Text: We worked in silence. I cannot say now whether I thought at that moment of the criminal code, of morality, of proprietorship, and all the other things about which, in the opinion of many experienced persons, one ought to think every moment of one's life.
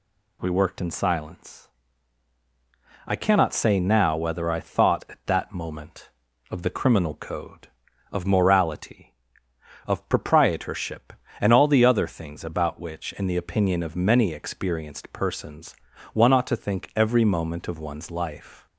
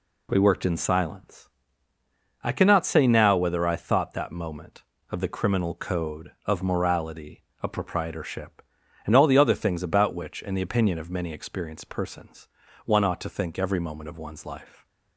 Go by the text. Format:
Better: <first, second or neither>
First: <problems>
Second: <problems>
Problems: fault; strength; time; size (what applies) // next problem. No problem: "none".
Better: first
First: none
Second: skips "at"; at 4.1 s